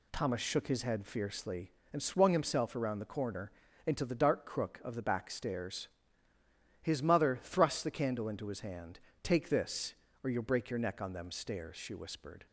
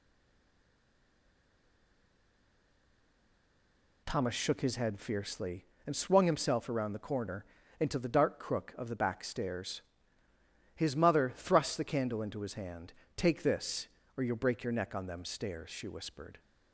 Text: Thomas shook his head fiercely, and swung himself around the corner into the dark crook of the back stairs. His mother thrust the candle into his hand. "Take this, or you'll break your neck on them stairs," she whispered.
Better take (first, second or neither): first